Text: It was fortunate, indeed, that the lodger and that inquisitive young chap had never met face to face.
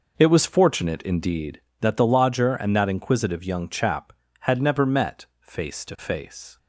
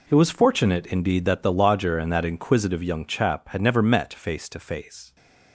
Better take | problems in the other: second | starts louder than the rest; noticeable; until 1.7 s; 5.5 dB // pauses between "met" and "face"; slight; at 5.2 s; 0.16 s long

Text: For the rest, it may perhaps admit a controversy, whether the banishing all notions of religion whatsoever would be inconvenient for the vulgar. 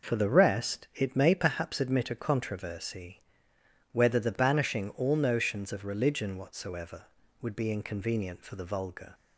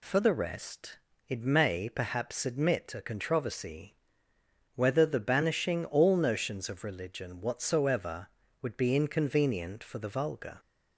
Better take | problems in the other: neither | none

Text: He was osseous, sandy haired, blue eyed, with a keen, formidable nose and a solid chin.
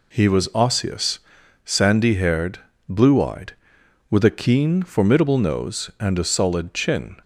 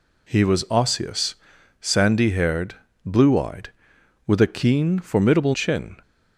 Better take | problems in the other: first | skips "nose and a solid"; at 5.5 s

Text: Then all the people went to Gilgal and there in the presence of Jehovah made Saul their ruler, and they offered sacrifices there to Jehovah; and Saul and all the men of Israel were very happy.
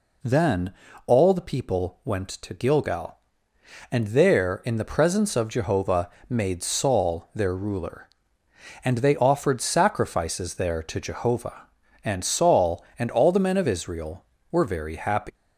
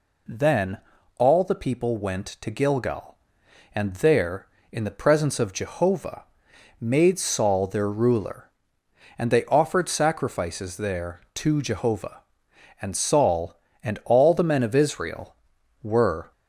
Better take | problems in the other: first | pauses between "Then" and "all"; at 0.7 s; 0.38 s long; slight in the first // pauses between "Jehovah" and "made"; noticeable; at 6.2 s; 0.56 s long; slight in the first // stops before "very happy"; at 16.3 s

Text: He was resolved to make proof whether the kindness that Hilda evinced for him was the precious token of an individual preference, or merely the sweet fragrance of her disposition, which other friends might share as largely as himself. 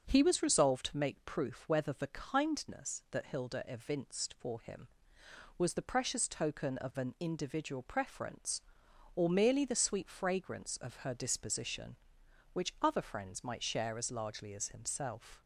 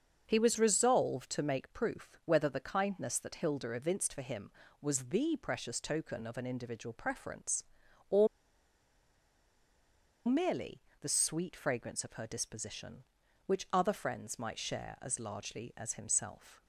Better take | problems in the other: first | starts louder than the rest; until 1.2 s; 6.5 dB; also in the first // pauses between "or" and "merely"; strong; at 8.2 s; 1.9 s long // pauses between "merely" and "the"; slight; at 10.8 s; 0.20 s long

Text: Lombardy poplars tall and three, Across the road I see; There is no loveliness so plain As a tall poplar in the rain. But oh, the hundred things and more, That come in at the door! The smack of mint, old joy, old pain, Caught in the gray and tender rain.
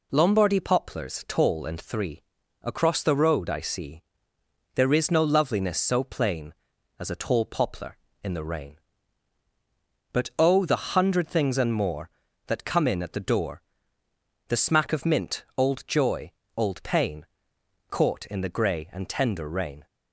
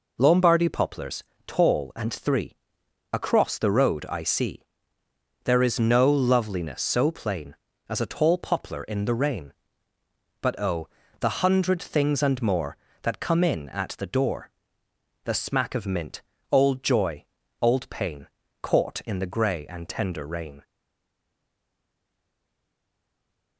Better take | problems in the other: first | pauses between "poplars" and "tall"; slight; at 1.2 s; 0.24 s long // stays silent after the last word; strong; from 20.6 s on; 2.9 s long

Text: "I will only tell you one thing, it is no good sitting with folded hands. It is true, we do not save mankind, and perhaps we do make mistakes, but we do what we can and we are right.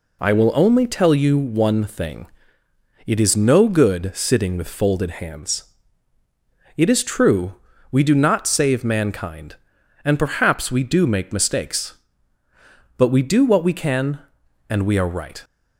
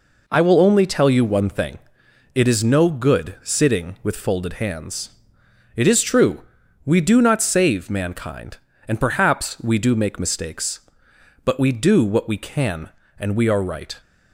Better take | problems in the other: neither | none

